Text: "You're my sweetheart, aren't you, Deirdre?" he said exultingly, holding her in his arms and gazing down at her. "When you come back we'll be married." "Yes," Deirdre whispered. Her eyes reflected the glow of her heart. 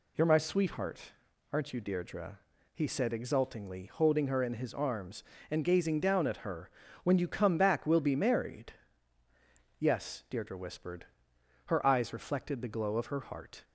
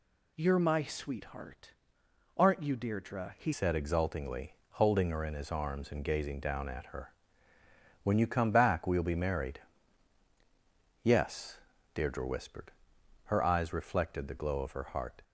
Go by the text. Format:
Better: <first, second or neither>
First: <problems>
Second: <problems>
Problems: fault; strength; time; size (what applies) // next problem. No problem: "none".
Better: first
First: none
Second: changes voice at "said"; from 3.5 s on; 11.7 s long